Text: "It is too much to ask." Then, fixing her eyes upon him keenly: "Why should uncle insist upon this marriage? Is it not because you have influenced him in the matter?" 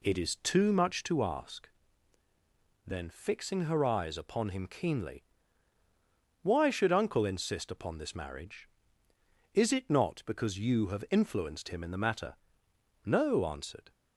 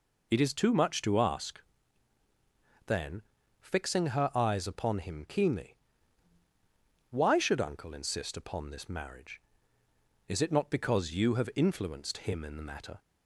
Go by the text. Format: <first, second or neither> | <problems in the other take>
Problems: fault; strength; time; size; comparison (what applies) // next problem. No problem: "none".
second | goes on to say "No answered"; noticeable; from 13.0 s on; 0.86 s long